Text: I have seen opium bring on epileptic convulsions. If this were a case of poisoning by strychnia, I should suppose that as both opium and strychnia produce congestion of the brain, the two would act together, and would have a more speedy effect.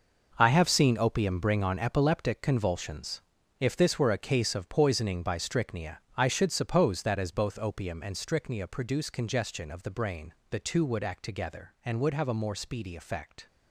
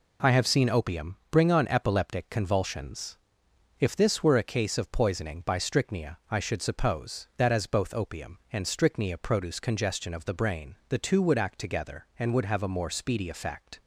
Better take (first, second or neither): second